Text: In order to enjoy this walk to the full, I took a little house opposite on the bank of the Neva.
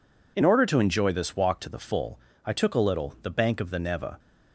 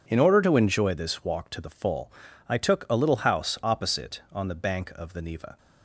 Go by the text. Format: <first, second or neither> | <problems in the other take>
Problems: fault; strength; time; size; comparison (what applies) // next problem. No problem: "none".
second | skips "house opposite on"; at 3.1 s